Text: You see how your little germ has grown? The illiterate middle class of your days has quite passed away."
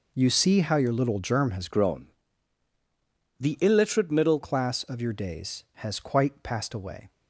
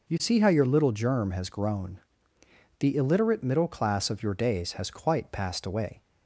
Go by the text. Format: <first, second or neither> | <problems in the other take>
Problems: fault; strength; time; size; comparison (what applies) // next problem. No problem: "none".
second | changes voice from "grown" to "middle"; from 1.7 to 4.3 s; 2.6 s long